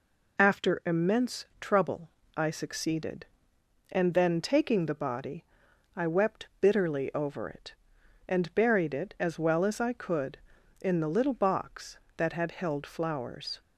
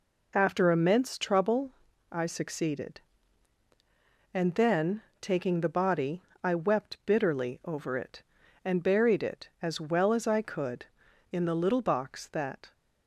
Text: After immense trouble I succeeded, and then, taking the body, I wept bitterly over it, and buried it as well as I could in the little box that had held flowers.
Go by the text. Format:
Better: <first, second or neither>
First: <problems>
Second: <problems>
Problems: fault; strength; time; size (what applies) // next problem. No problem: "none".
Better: first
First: pauses between "trouble" and "I"; slight; at 2.1 s; 0.26 s long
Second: pauses between "trouble" and "I"; at 1.7 s; 0.40 s long // stops before "had held flowers"; at 12.7 s